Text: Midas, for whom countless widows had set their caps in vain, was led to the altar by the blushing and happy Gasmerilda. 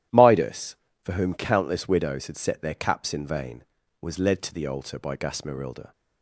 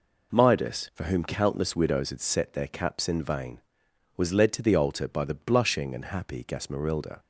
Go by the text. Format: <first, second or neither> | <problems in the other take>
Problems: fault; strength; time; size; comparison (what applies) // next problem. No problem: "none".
second | starts louder than the rest; strong; until 1.4 s; 12.5 dB // skips "the blushing and happy"; at 5.1 s